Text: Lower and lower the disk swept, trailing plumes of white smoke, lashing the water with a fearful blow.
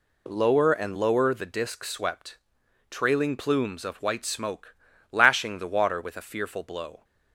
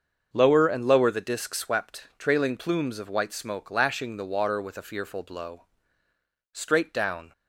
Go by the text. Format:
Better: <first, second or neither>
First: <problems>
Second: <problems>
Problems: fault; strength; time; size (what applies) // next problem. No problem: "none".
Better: first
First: none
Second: starts louder than the rest; until 1.3 s; 6.5 dB // goes on to say "Straight down"; noticeable; from 6.5 s on; 0.80 s long